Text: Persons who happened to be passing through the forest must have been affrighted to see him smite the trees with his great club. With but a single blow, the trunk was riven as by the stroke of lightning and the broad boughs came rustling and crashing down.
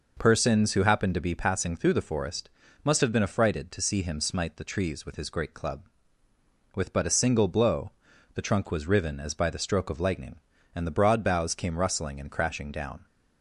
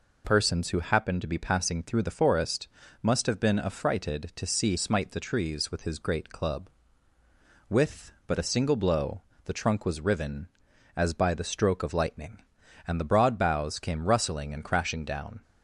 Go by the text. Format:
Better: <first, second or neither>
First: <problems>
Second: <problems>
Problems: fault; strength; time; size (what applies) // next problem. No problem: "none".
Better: first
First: pauses between "forest" and "must"; slight; at 2.4 s; 0.34 s long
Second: pauses between "forest" and "must"; slight; at 2.6 s; 0.34 s long // skips "him"; at 4.7 s